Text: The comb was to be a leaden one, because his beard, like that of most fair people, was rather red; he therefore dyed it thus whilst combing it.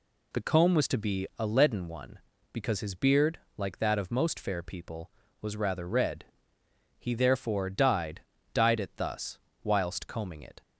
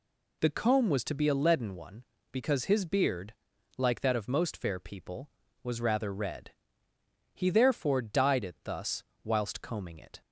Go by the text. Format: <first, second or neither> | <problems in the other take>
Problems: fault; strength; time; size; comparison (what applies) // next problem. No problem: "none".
second | says "dyed" twice; at 8.5 s // pauses between "thus" and "whilst"; slight; at 9.3 s; 0.22 s long; slight in the second